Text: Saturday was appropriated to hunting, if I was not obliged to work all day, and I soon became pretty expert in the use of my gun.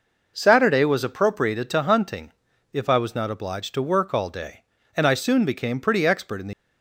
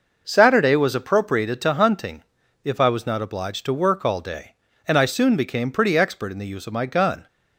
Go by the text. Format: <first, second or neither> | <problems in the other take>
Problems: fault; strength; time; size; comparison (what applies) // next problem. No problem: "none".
second | stops before "use of my gun"; at 6.5 s